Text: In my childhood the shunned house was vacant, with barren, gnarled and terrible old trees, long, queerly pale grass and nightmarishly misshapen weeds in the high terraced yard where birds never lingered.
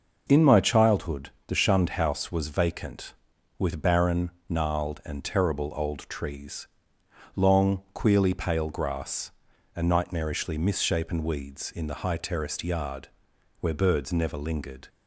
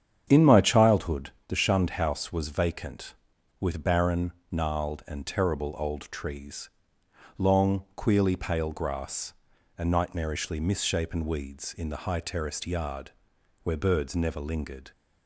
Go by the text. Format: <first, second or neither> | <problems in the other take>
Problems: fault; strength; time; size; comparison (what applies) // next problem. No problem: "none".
first | starts louder than the rest; strong; until 1.5 s; 8.5 dB // pauses between "childhood" and "the"; slight; at 1.3 s; 0.16 s long; slight in the first // pauses between "yard" and "where"; noticeable; at 13.0 s; 0.54 s long; noticeable in the first